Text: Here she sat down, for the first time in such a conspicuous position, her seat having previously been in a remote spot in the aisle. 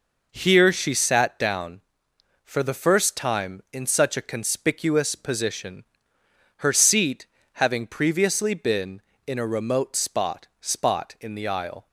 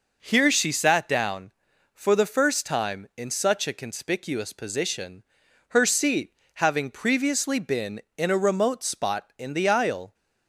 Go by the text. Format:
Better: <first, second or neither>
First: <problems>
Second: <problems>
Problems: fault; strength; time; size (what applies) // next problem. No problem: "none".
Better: second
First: pauses between "seat" and "having"; slight; at 7.2 s; 0.28 s long // says "spot" twice; at 10.6 s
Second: pauses between "seat" and "having"; slight; at 6.3 s; 0.20 s long